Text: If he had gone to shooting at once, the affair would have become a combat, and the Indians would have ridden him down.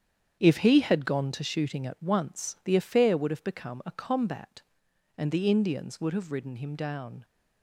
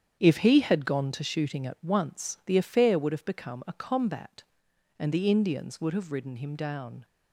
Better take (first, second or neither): neither